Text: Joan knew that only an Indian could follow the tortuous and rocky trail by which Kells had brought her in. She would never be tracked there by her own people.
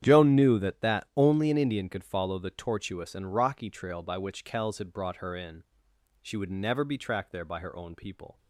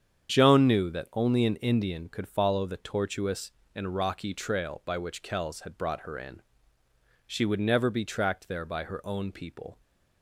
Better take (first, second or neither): second